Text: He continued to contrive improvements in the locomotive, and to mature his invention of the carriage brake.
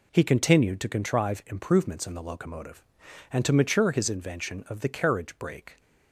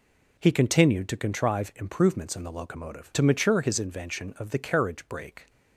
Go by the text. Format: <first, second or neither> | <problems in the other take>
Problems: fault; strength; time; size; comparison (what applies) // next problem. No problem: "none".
first | skips "and"; at 3.1 s